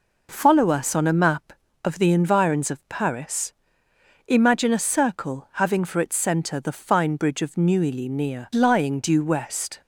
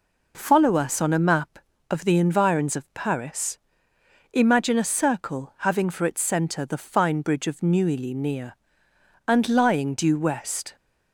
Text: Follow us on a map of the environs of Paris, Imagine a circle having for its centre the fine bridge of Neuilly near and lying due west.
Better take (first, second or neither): second